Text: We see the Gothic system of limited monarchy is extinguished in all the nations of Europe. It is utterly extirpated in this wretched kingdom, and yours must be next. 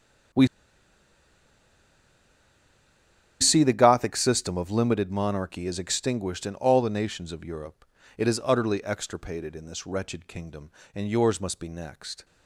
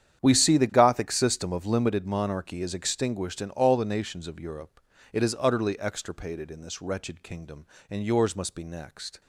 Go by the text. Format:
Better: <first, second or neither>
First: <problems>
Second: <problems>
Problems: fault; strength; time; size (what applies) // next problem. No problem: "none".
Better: second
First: starts louder than the rest; strong; until 4.2 s; 9 dB // pauses between "We" and "see"; strong; at 0.4 s; 2.9 s long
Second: starts louder than the rest; strong; until 1.2 s; 9 dB